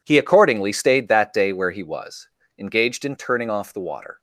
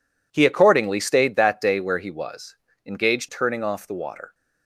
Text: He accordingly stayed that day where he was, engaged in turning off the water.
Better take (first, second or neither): first